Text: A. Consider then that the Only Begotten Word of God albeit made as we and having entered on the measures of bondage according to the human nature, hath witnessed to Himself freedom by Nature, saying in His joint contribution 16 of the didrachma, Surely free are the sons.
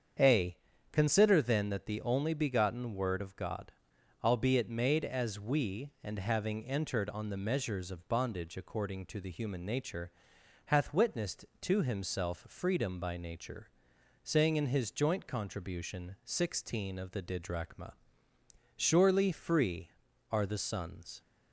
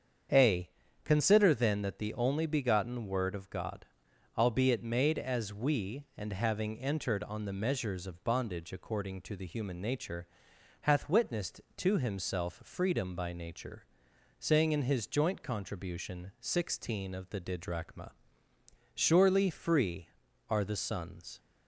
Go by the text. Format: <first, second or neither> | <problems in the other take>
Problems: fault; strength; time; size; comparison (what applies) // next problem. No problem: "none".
neither | starts louder than the rest; strong; the same in both // pauses between "God" and "albeit"; noticeable; the same in both